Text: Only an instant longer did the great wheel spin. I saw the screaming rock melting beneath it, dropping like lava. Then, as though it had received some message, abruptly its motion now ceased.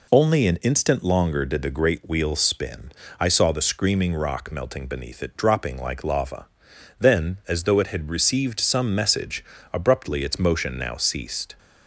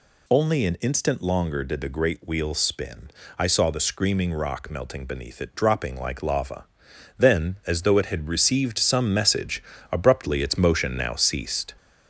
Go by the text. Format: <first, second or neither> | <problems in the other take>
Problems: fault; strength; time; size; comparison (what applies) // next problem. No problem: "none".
first | gets louder; throughout; 3.5 dB